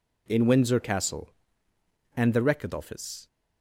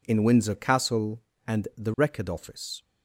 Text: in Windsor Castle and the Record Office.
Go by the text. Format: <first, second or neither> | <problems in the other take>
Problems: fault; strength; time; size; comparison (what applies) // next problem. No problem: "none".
neither | none